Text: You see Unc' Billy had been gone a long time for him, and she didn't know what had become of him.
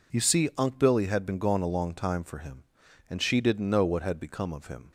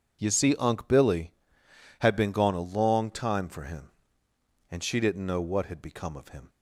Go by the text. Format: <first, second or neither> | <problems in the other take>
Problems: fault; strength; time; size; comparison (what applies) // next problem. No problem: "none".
neither | none